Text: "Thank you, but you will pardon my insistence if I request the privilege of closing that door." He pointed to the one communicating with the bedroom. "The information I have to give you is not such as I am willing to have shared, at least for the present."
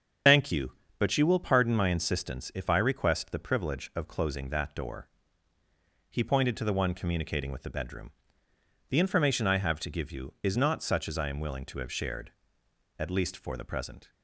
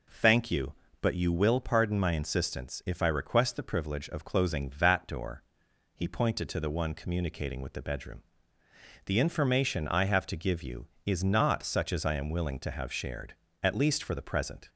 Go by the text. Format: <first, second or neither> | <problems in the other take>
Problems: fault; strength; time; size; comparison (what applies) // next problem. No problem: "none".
second | loses the start of "Thank"; at 0.2 s; 125 ms // starts louder than the rest; strong; until 1.5 s; 7 dB